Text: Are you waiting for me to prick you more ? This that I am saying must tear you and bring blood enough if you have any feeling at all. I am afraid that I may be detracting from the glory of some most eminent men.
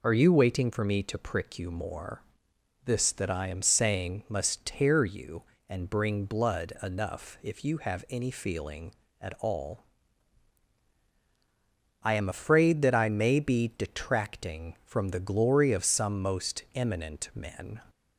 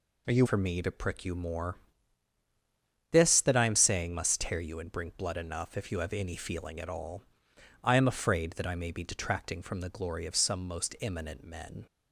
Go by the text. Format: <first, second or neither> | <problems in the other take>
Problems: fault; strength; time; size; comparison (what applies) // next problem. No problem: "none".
first | skips "waiting"; at 0.4 s